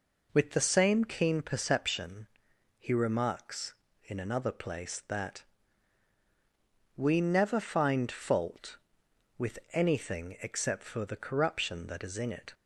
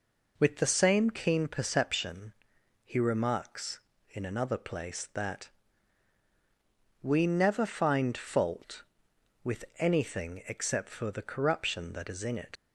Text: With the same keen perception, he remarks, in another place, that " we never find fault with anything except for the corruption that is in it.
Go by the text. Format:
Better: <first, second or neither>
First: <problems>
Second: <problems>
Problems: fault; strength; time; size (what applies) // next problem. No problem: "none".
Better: first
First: none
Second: leaves "it" unfinished; at 12.5 s; 40 ms